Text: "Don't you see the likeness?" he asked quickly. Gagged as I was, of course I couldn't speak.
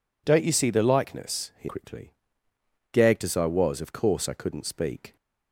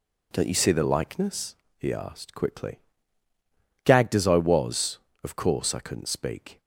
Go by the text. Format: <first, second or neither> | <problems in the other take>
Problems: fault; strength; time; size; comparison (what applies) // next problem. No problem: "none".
second | skips "asked"; at 1.6 s